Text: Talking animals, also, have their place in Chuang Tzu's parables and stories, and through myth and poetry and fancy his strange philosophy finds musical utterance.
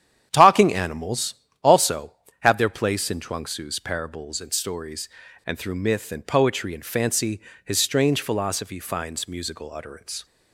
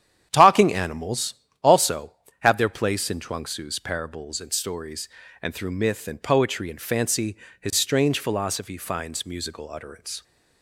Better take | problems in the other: neither | starts louder than the rest; strong; the same in both // pauses between "fancy" and "his"; slight; the same in both

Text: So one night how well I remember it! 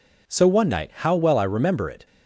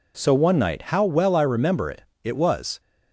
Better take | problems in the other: first | goes on to say "it was"; from 2.2 s on; 0.56 s long

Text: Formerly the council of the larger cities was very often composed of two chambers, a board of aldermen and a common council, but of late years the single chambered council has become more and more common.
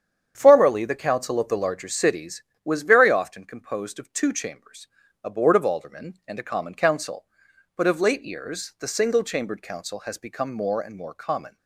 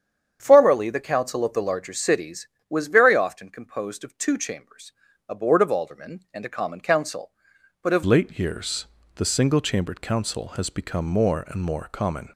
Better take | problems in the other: first | starts louder than the rest; strong; until 1.4 s; 8 dB; strong in the first // changes voice at "late"; from 8.0 s on; 4.2 s long // pauses between "years" and "the"; slight; at 8.8 s; 0.32 s long

